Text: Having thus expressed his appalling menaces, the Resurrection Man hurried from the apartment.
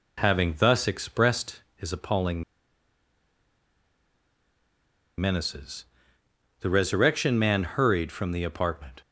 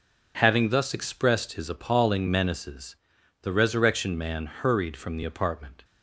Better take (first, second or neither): second